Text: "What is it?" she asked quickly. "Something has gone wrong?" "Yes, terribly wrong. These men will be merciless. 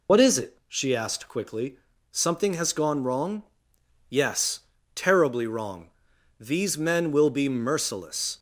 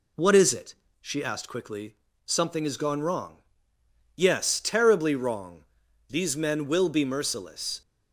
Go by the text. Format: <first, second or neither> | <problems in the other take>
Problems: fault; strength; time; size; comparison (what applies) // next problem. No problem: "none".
second | loses the start of "What"; at 0.0 s; 70 ms